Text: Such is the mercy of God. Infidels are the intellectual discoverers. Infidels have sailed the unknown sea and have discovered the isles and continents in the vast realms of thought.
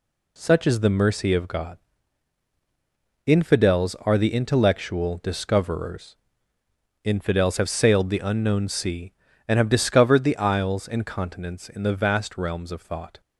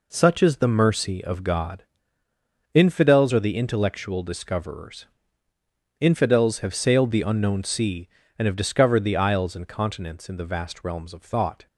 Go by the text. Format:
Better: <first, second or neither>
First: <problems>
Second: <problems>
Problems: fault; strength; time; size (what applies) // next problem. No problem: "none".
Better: neither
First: none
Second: none